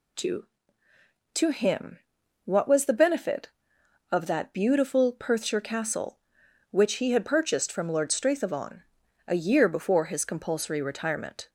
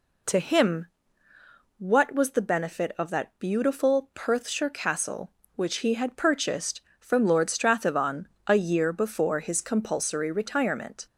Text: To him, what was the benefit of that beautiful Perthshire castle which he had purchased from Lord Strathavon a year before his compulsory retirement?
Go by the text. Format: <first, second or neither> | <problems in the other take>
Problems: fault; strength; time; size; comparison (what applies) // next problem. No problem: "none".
second | says "To" twice; at 1.3 s // pauses between "Strathavon" and "a"; at 8.8 s; 0.44 s long; slight in the second